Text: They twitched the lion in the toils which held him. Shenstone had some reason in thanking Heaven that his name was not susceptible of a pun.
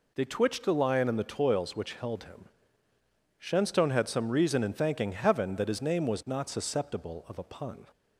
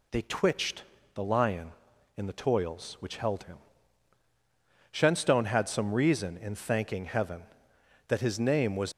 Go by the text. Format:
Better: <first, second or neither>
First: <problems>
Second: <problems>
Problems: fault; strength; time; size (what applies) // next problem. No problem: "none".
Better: first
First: none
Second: pauses between "twitched" and "the"; slight; at 0.8 s; 0.30 s long // stops before "not susceptible of a pun"; at 8.9 s